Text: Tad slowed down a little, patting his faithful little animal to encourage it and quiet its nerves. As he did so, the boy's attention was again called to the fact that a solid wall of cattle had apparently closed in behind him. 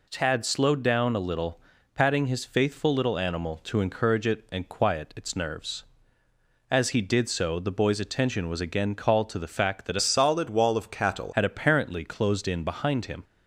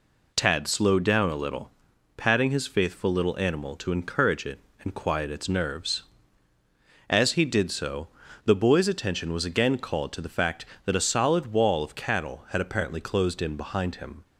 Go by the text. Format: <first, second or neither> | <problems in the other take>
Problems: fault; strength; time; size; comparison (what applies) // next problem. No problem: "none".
second | changes voice from "solid" to "cattle"; from 9.9 to 11.3 s; 1.4 s long